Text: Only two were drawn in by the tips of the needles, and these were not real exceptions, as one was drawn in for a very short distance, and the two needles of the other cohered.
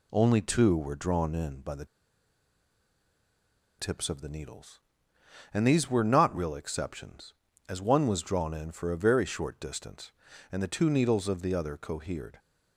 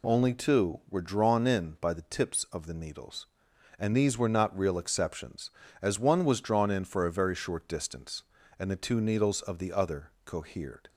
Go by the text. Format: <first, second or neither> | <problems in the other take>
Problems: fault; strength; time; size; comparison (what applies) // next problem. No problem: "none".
second | pauses between "the" and "tips"; strong; at 1.8 s; 1.9 s long